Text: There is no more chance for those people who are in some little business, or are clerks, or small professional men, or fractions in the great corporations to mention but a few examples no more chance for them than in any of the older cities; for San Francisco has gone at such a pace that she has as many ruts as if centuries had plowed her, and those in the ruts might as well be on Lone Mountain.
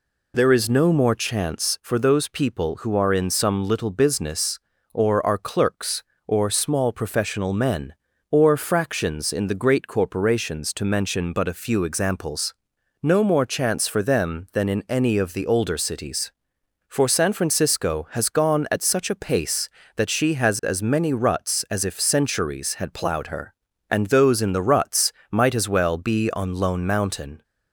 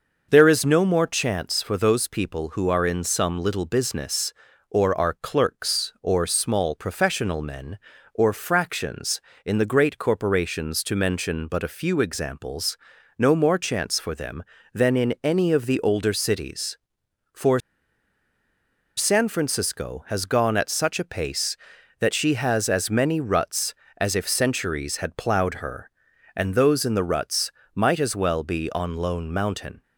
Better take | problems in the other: first | pauses between "examples" and "no"; at 12.7 s; 0.40 s long; noticeable in the first // pauses between "for" and "San"; strong; at 17.5 s; 1.3 s long // pauses between "ruts" and "might"; slight; at 27.4 s; 0.24 s long; slight in the first

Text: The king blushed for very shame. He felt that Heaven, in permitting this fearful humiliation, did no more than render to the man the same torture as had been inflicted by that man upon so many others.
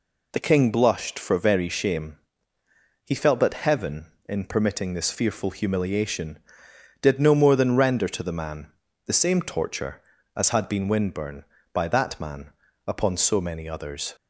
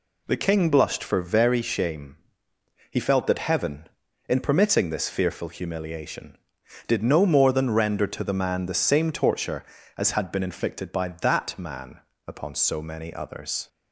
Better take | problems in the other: second | pauses between "man" and "the"; at 8.6 s; 0.38 s long // says "windburn" for "inflicted"; at 10.8 s // pauses between "man" and "upon"; slight; at 12.5 s; 0.34 s long; slight in the second

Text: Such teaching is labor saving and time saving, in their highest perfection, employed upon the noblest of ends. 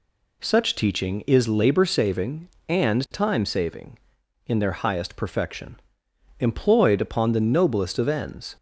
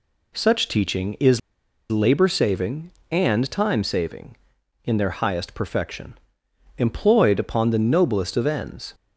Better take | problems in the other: first | pauses between "is" and "labor"; noticeable; at 1.3 s; 0.52 s long

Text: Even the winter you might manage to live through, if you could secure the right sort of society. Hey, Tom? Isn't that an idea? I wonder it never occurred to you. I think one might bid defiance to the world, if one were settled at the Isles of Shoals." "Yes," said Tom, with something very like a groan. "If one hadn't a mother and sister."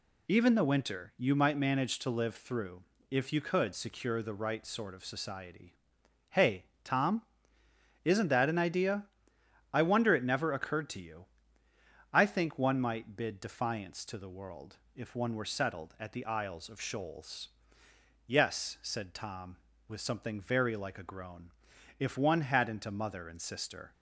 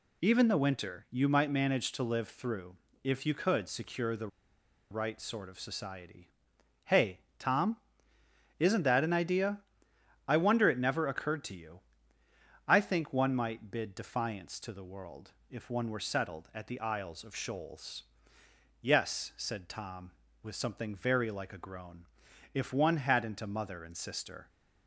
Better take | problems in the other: first | pauses between "the" and "right"; noticeable; at 4.2 s; 0.63 s long

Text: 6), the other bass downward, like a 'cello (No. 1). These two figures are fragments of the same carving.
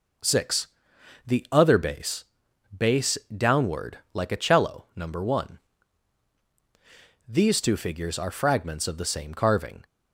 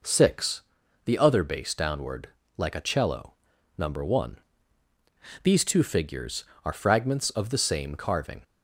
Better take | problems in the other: second | says "bass" twice; at 2.7 s

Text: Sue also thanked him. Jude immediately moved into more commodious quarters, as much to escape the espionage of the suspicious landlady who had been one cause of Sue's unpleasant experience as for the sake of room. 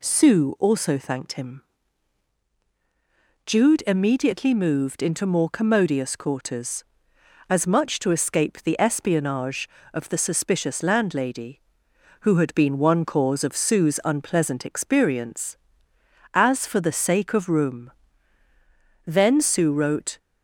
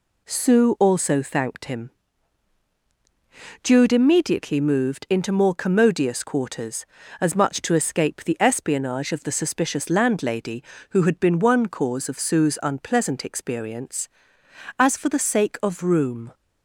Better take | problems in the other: second | goes on to say "Then Sue wrote"; noticeable; from 19.0 s on; 1.1 s long

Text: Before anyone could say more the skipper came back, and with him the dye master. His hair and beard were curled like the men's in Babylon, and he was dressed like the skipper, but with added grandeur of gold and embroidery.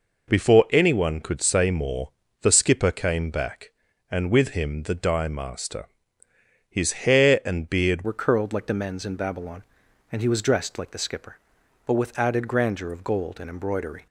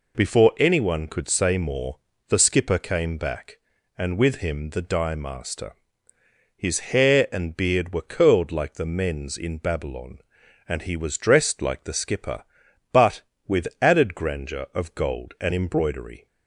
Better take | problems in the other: second | pauses between "more" and "the"; slight; at 2.1 s; 0.32 s long; slight in the second // changes voice at "were"; from 8.0 s on; 6.0 s long

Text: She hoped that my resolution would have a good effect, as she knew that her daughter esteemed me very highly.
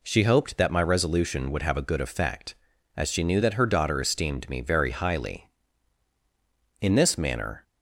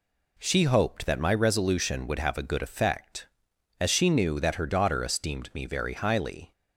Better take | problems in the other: second | goes on to say "In this manner"; noticeable; from 6.8 s on; 0.82 s long

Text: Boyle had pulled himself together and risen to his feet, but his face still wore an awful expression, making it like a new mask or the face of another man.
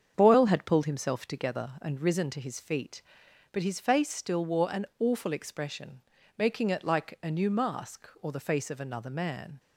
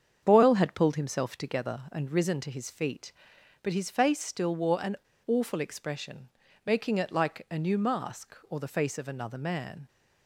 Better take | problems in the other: first | starts louder than the rest; strong; until 1.2 s; 7.5 dB; strong in the first // pauses between "an" and "awful"; slight; at 4.9 s; 0.31 s long

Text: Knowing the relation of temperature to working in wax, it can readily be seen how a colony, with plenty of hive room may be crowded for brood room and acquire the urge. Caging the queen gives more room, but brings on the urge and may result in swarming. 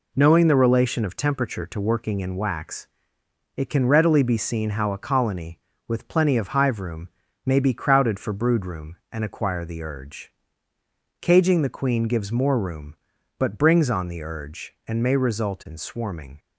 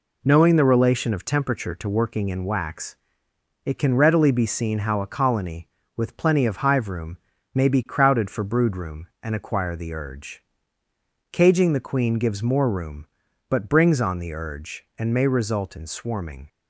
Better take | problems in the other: neither | pauses between "room" and "may"; the same in both

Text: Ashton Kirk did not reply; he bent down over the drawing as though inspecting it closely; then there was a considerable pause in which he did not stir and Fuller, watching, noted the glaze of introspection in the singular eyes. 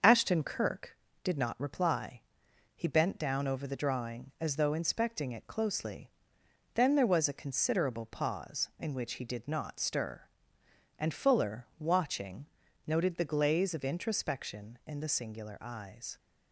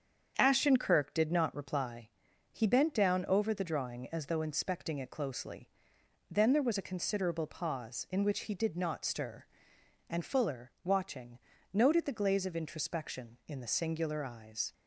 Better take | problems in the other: neither | starts louder than the rest; the same in both

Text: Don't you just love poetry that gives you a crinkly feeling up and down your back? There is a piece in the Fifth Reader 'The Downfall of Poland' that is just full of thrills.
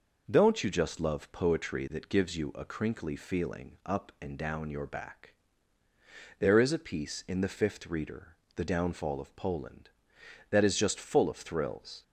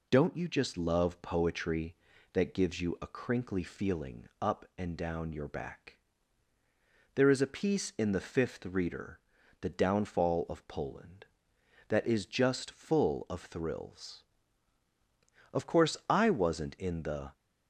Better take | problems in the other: first | pauses between "Reader" and "The"; at 9.1 s; 0.42 s long; slight in the first // goes on to say "Of course I wasn't in the"; strong; from 15.5 s on; 1.8 s long

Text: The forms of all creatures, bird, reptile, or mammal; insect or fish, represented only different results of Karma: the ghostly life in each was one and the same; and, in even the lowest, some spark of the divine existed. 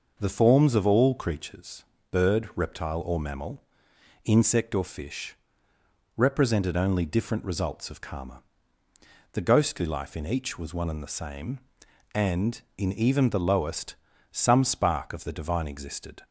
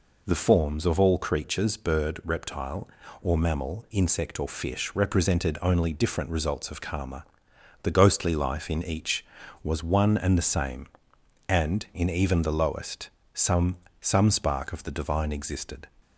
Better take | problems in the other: first | says "some" twice; at 14.0 s

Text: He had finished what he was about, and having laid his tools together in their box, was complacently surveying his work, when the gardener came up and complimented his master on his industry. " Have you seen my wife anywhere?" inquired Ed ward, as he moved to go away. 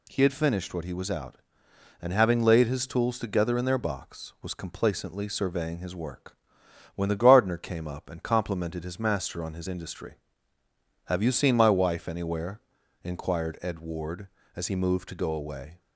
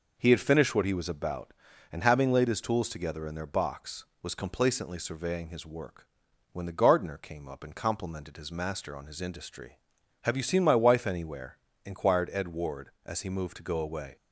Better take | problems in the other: second | says "out" for "about"; at 1.1 s

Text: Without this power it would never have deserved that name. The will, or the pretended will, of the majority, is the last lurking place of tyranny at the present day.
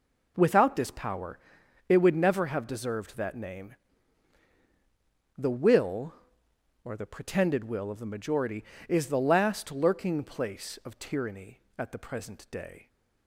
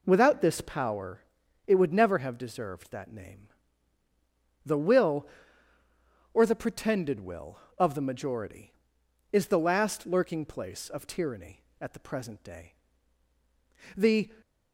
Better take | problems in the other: first | pauses between "power" and "it"; noticeable; at 1.2 s; 0.46 s long; noticeable in the first // goes on to say "The"; slight; from 13.9 s on; 0.32 s long

